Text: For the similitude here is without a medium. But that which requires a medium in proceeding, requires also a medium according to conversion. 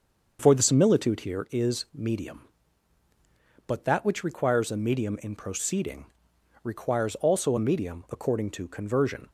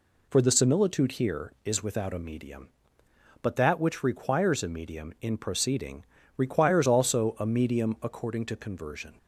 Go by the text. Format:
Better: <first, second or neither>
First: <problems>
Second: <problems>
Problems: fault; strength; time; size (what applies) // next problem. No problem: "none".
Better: second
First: starts louder than the rest; until 1.4 s; 6.5 dB // skips "without a"; at 1.8 s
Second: none